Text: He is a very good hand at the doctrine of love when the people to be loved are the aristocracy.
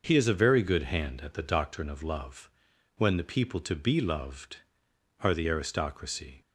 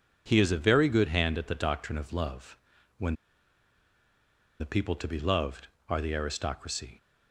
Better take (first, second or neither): first